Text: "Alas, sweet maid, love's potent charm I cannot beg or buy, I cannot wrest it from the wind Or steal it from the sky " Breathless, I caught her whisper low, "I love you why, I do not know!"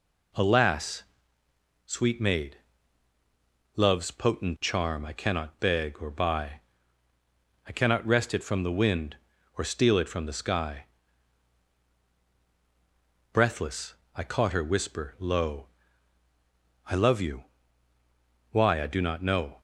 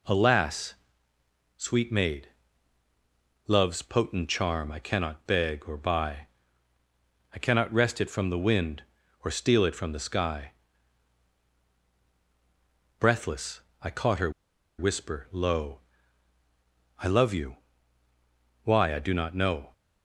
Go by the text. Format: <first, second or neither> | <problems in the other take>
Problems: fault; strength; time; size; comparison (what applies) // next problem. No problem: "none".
first | pauses between "her" and "whisper"; noticeable; at 14.3 s; 0.47 s long // pauses between "you" and "why"; at 17.5 s; 1.0 s long; also in the first